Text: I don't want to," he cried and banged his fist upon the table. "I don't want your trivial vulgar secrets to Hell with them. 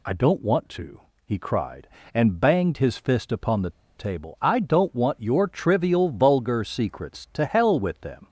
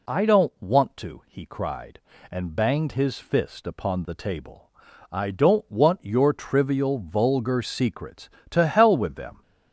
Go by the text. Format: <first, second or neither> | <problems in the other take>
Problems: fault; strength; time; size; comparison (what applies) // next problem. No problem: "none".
second | pauses between "the" and "table"; slight; at 3.6 s; 0.27 s long